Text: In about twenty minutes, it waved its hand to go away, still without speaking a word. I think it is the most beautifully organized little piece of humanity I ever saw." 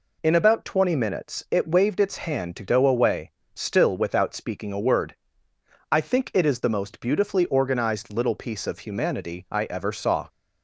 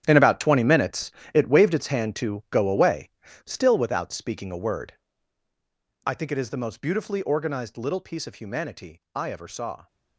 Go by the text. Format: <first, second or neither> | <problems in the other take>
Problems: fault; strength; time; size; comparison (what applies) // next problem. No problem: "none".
first | gets quieter; strong; throughout; 14 dB